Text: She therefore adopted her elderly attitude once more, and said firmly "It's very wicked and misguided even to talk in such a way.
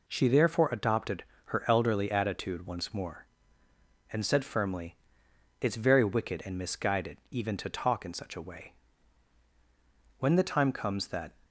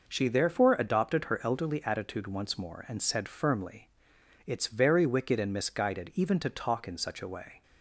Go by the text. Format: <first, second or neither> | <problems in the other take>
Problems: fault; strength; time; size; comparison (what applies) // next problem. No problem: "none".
second | pauses between "adopted" and "her"; slight; at 1.2 s; 0.22 s long // pauses between "firmly" and "It's"; noticeable; at 4.9 s; 0.64 s long; noticeable in the second // goes on to say "When the time comes that"; noticeable; from 10.1 s on; 1.1 s long